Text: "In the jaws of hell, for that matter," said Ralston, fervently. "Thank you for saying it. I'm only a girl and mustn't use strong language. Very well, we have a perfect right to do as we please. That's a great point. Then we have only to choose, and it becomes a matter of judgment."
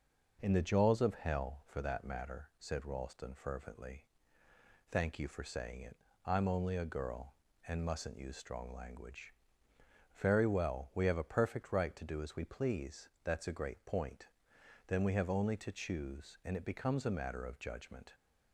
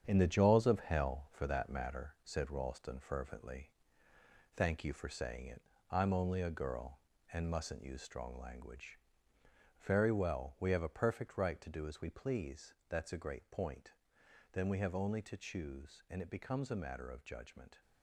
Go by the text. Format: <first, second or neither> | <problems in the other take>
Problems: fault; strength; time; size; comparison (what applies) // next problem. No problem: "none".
first | gets quieter; strong; throughout; 8 dB